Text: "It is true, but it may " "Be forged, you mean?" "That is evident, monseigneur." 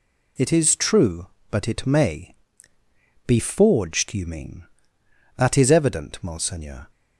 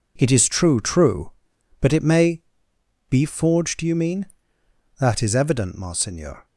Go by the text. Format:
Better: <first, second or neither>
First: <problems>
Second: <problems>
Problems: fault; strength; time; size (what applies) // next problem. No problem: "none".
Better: first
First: none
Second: says "true" twice; at 0.8 s